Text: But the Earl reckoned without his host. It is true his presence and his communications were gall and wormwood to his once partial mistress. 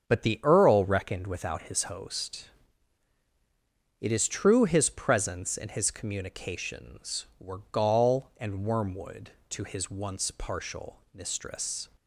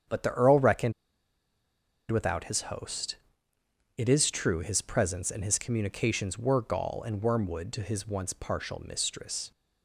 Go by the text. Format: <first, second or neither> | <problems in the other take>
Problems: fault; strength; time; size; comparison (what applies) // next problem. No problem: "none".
first | starts louder than the rest; strong; until 2.2 s; 8 dB; strong in the first // pauses between "reckoned" and "without"; at 0.9 s; 1.1 s long